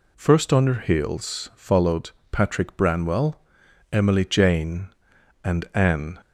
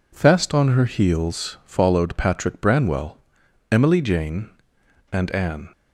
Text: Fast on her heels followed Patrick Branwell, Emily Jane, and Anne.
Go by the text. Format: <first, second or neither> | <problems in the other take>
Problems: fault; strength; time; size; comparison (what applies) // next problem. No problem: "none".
second | says "First" for "Fast"; at 0.1 s // pauses between "followed" and "Patrick"; slight; at 2.1 s; 0.20 s long